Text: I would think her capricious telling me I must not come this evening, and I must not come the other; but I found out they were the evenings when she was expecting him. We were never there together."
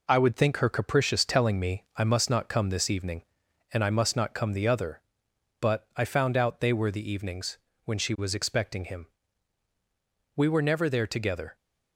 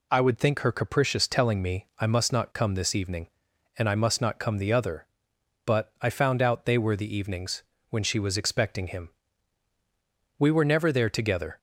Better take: second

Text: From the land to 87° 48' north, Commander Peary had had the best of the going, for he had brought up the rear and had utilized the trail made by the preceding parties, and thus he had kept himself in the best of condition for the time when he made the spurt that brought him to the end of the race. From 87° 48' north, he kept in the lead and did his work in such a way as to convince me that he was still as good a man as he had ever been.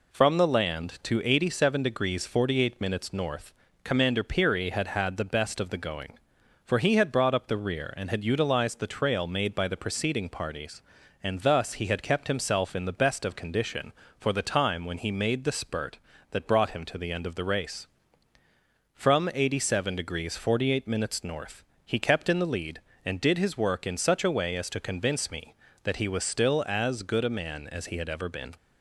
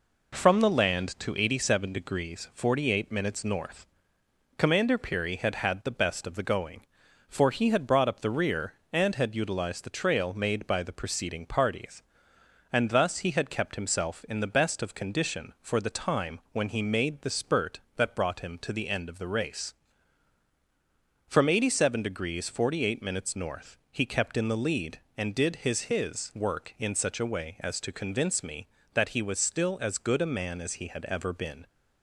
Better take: first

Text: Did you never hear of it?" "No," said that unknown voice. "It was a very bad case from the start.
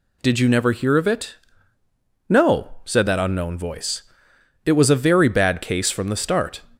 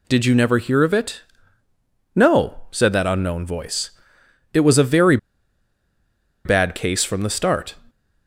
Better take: first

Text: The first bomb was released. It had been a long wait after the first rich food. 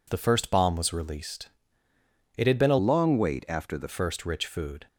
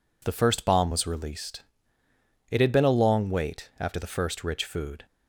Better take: second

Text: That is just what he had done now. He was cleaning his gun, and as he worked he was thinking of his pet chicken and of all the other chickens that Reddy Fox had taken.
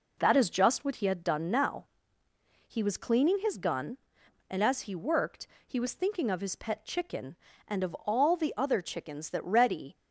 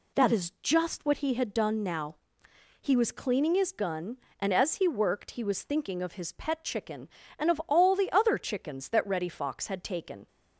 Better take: second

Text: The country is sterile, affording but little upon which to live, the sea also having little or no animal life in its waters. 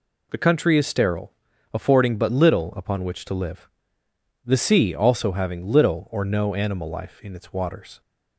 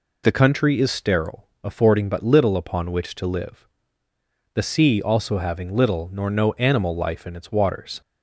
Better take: first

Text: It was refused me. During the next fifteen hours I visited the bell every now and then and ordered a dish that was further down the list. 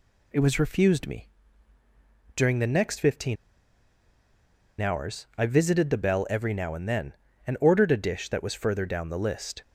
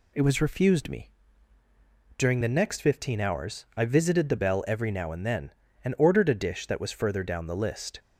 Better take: second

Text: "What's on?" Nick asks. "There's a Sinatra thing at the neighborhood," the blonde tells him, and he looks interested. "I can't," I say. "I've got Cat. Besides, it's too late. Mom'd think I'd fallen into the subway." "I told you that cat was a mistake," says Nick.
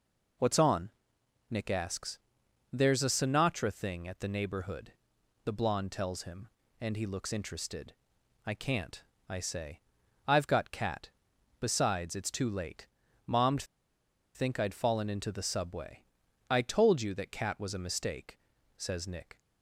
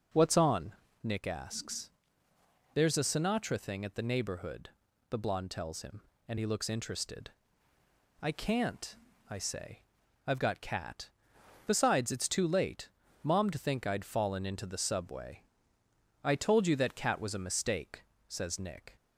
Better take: second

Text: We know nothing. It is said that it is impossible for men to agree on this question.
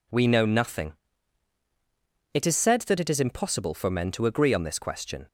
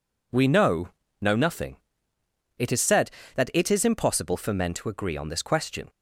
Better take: first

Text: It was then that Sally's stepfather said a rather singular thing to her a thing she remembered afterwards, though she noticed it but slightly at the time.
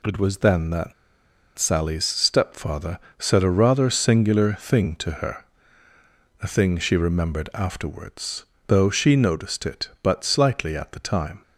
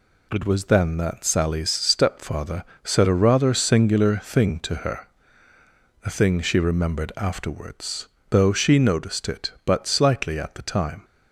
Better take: second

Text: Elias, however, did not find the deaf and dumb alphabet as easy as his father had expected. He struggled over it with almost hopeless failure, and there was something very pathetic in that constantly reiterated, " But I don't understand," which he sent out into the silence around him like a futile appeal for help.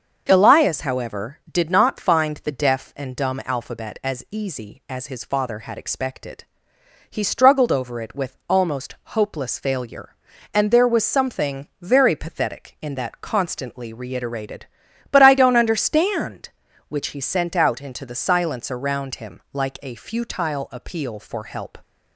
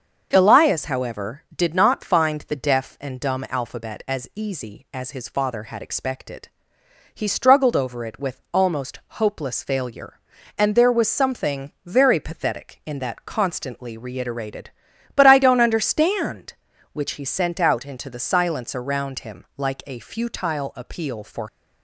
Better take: first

